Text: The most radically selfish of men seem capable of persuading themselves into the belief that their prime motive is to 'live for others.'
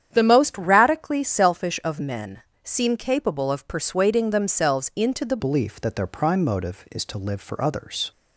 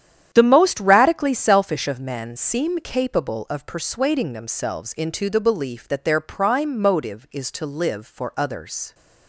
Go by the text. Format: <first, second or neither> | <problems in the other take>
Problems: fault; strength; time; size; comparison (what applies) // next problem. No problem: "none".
second | starts louder than the rest; strong; until 1.1 s; 9 dB; strong in the second // pauses between "men" and "seem"; slight; at 2.4 s; 0.22 s long // changes voice at "belief"; from 5.3 s on; 2.8 s long